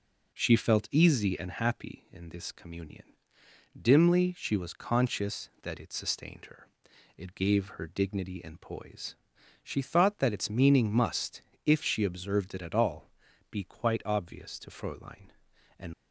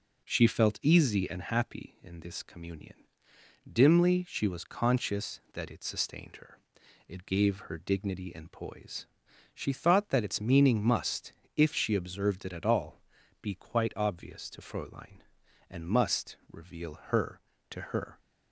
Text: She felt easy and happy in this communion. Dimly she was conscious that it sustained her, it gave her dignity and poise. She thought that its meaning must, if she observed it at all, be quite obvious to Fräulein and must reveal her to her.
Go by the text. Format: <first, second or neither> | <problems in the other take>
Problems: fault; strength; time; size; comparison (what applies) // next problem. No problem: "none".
second | stops before "must reveal her to her"; at 15.9 s